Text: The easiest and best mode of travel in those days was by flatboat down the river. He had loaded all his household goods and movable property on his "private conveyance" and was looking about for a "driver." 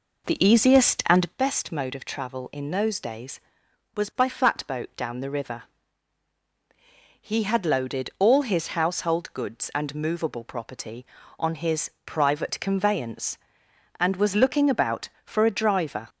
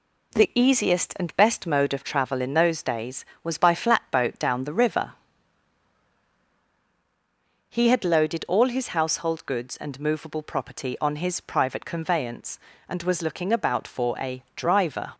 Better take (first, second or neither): second